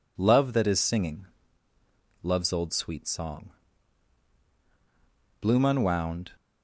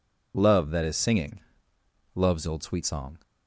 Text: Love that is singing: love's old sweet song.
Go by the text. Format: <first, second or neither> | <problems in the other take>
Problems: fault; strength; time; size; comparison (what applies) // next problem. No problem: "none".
second | goes on to say "Bloom unwound"; noticeable; from 5.4 s on; 0.94 s long